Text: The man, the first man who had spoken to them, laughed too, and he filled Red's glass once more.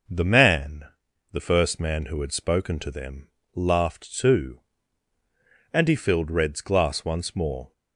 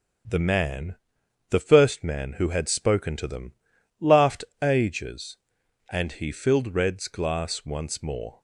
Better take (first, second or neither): first